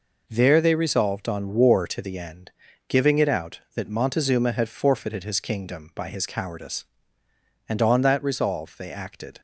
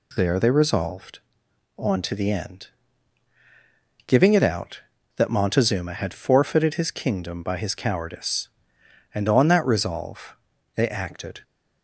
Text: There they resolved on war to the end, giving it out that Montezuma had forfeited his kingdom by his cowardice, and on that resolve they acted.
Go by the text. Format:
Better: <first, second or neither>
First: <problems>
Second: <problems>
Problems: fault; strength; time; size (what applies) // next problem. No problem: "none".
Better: first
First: none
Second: skips "war"; at 2.0 s // pauses between "resolve" and "they"; at 10.3 s; 0.40 s long